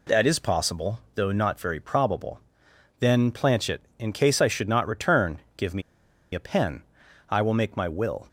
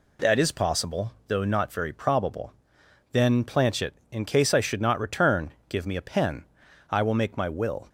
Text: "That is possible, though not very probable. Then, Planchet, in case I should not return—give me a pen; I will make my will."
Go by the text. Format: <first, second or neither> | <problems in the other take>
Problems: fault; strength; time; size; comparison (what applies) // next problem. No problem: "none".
second | pauses between "me" and "a"; noticeable; at 5.8 s; 0.52 s long